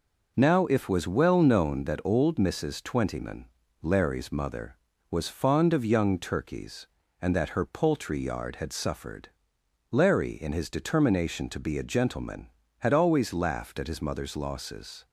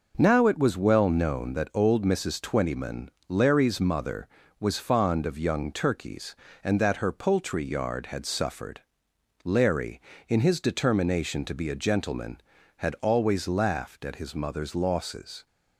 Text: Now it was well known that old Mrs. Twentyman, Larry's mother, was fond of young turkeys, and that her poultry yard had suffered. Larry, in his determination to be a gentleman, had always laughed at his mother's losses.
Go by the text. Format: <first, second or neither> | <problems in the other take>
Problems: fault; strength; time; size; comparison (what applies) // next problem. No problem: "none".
second | says "if" for "it"; at 0.6 s